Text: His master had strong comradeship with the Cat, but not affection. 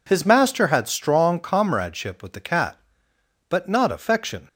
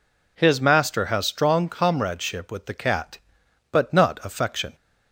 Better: first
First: none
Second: says "has" for "had"; at 1.0 s

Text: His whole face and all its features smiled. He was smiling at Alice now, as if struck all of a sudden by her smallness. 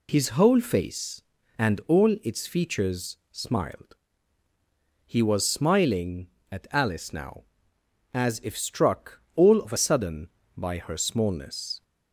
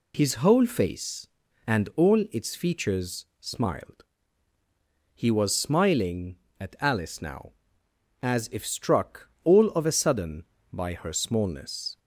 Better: second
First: pauses between "struck" and "all"; slight; at 9.1 s; 0.16 s long // changes voice from "of" to "a"; from 9.6 to 9.7 s; 0.1 s long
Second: pauses between "struck" and "all"; slight; at 9.2 s; 0.16 s long

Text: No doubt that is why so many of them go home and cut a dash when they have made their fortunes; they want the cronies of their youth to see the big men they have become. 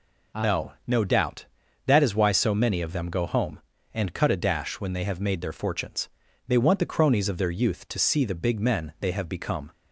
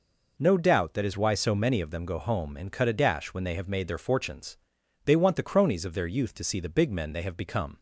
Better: second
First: says "No" twice; at 0.8 s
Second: none

